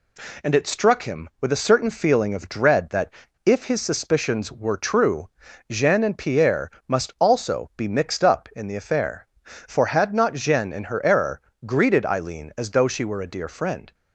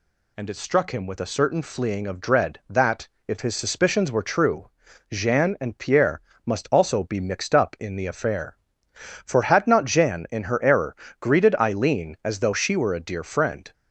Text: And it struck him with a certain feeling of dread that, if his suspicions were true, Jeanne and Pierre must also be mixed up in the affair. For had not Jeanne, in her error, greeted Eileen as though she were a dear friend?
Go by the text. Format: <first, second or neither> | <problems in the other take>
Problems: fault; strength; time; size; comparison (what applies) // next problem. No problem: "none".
first | says "fleeing" for "feeling"; at 1.6 s // pauses between "Pierre" and "must"; slight; at 6.1 s; 0.24 s long; slight in the first